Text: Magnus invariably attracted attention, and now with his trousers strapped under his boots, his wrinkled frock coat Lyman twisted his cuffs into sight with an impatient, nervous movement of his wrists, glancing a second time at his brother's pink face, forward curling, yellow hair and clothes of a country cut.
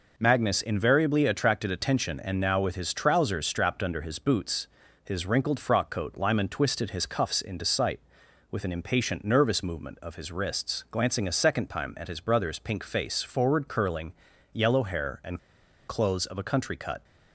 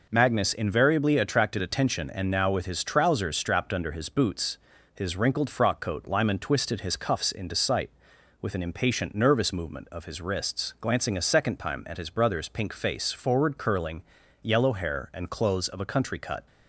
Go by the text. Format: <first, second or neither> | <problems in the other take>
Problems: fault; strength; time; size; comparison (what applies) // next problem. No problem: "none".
second | pauses between "and" and "clothes"; noticeable; at 15.3 s; 0.47 s long